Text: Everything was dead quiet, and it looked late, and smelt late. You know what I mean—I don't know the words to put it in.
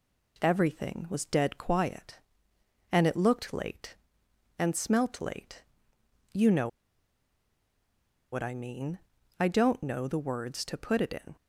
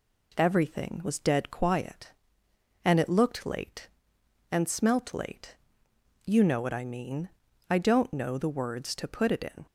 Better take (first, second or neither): second